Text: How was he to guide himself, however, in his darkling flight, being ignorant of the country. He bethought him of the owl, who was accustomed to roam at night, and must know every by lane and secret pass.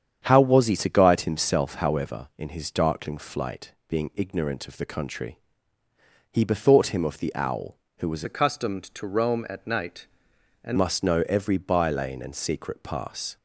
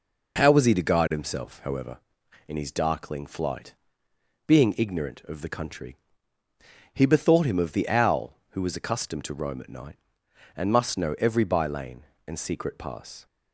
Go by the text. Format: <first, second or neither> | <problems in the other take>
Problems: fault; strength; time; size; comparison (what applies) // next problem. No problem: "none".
second | starts louder than the rest; strong; until 1.2 s; 8 dB // changes voice from "accustomed" to "and"; from 8.2 to 10.7 s; 2.5 s long